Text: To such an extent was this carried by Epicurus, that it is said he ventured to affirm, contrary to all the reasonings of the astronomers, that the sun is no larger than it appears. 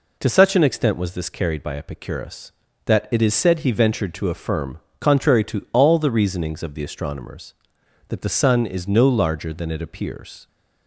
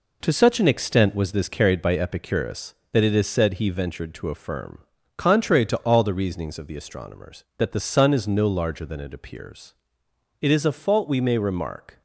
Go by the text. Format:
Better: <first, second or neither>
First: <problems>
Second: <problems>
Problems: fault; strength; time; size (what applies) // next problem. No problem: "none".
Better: first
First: none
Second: goes on to say "It is a fault we may remark"; from 10.3 s on; 1.6 s long